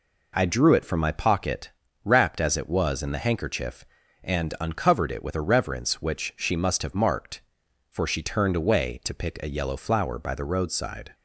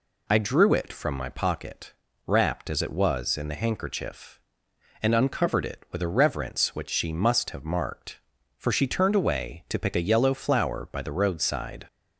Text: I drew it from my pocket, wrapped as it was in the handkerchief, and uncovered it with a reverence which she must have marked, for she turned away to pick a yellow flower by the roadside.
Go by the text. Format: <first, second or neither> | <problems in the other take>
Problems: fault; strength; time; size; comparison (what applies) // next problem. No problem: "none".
neither | none